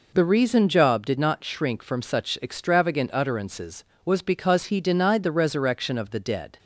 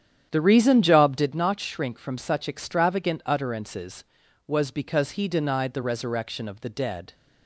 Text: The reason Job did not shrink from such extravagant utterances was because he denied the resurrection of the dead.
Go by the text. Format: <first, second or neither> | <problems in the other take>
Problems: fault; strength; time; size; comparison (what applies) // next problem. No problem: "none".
first | starts louder than the rest; strong; until 1.4 s; 9.5 dB